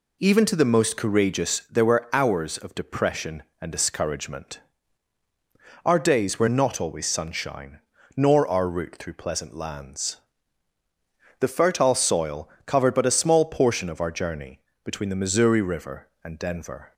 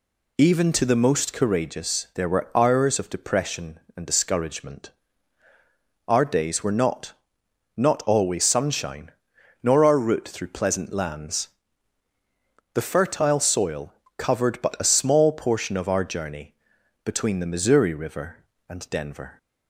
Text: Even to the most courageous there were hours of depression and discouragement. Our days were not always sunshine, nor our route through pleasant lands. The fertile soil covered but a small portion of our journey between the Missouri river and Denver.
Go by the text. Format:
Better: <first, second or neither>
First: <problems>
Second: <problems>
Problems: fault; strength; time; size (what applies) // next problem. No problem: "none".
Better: first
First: pauses between "soil" and "covered"; slight; at 12.4 s; 0.16 s long // pauses between "journey" and "between"; slight; at 14.5 s; 0.24 s long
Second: says "not" twice; at 7.7 s // pauses between "soil" and "covered"; slight; at 13.9 s; 0.24 s long // pauses between "journey" and "between"; noticeable; at 16.5 s; 0.52 s long